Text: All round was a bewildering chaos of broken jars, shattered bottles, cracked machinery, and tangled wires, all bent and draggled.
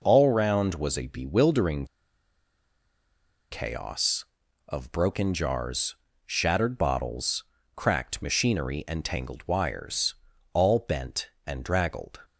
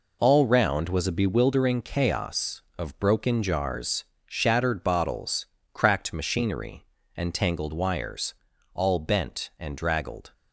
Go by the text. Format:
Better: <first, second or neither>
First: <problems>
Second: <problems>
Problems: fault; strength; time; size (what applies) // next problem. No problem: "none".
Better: second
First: pauses between "bewildering" and "chaos"; strong; at 1.8 s; 1.6 s long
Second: none